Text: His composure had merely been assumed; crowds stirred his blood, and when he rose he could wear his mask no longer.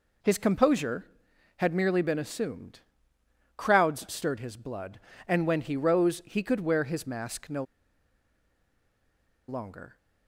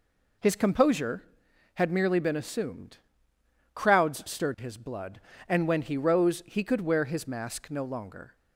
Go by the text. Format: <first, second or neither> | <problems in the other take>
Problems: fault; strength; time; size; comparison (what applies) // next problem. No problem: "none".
second | pauses between "no" and "longer"; strong; at 7.6 s; 1.8 s long